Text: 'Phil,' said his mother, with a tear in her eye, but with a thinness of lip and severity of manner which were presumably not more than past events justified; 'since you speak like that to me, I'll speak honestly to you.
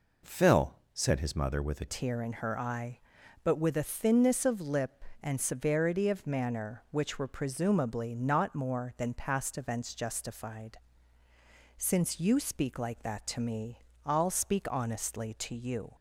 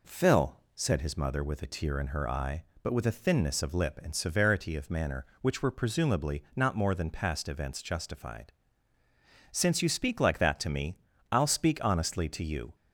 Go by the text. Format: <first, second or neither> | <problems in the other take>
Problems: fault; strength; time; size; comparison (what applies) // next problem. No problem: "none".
second | changes voice at "tear"; from 1.8 s on; 14.1 s long